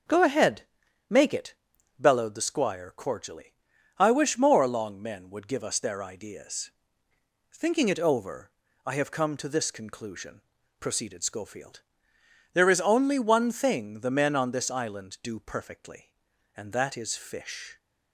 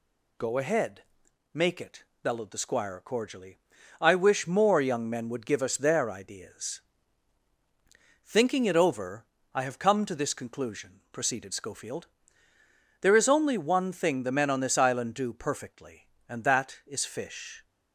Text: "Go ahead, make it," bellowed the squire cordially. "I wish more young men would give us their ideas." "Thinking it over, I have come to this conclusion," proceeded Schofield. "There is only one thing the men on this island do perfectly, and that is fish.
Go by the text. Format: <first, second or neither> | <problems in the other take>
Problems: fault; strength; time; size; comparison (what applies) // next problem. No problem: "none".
second | starts louder than the rest; until 1.5 s; 6.5 dB // says "long" for "young"; at 4.6 s